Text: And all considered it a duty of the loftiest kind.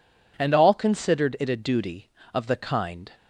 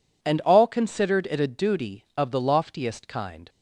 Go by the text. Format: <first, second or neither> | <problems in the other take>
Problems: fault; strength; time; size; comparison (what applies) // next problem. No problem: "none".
second | skips "loftiest"; at 2.5 s